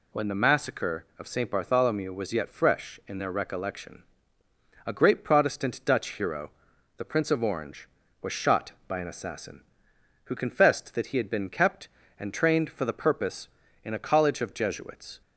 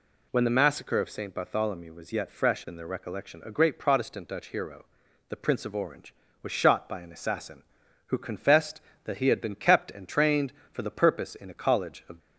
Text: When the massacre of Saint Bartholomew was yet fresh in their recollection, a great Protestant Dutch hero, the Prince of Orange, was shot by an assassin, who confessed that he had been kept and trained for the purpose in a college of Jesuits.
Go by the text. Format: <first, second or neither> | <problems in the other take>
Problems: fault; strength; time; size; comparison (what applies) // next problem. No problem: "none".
first | stops before "Jesuits"; at 12.1 s